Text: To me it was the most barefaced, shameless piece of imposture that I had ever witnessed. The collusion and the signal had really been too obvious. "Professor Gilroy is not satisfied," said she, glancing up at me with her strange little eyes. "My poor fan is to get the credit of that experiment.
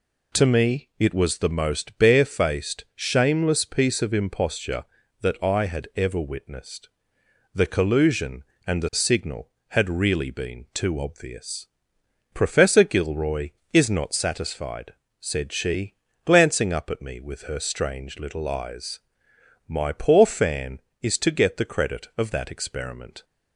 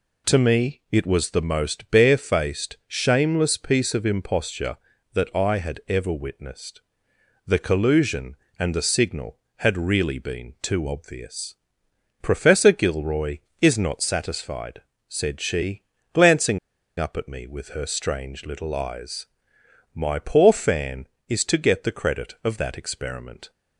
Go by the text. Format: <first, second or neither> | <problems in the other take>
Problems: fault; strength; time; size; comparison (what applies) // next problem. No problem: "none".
first | pauses between "glancing" and "up"; at 16.5 s; 0.40 s long